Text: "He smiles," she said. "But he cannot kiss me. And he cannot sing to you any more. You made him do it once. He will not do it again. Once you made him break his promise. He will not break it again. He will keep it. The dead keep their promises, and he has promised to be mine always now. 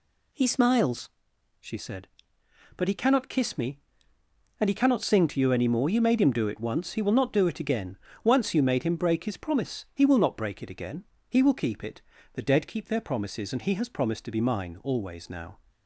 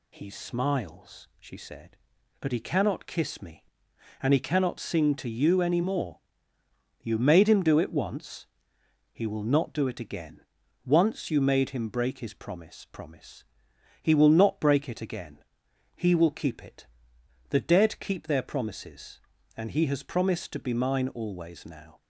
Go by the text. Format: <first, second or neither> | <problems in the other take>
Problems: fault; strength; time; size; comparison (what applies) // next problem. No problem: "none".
first | says "promise" twice; at 12.9 s